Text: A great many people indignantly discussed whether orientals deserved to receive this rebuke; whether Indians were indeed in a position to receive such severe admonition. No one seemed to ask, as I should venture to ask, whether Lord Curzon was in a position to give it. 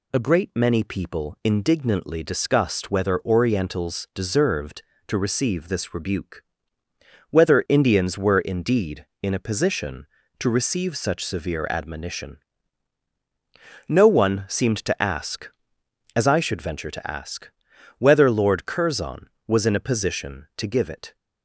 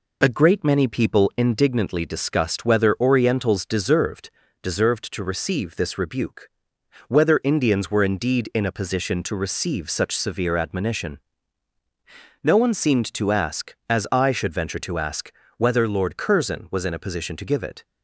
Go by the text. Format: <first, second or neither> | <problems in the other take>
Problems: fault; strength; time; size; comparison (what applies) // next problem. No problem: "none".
first | says "deserved" twice; at 4.6 s